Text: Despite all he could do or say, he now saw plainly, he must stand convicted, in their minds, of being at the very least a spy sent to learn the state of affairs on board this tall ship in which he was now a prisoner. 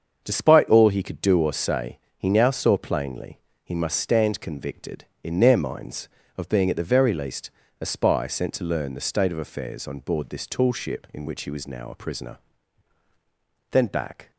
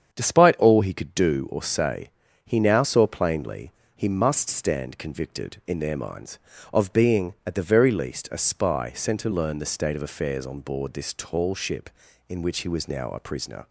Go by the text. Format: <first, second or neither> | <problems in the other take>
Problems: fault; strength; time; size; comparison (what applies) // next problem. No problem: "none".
second | starts louder than the rest; until 1.2 s; 6.5 dB; strong in the second // pauses between "least" and "a"; slight; at 7.5 s; 0.30 s long // goes on to say "Then back"; from 13.7 s on; 0.60 s long